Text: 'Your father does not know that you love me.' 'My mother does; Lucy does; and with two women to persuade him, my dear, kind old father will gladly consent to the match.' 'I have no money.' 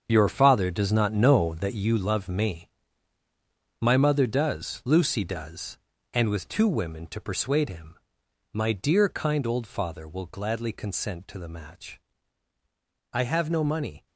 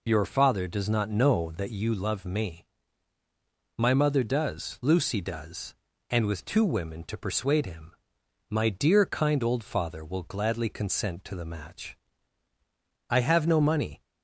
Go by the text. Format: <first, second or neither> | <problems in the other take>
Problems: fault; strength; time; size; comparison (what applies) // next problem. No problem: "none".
second | gets quieter; strong; throughout; 11 dB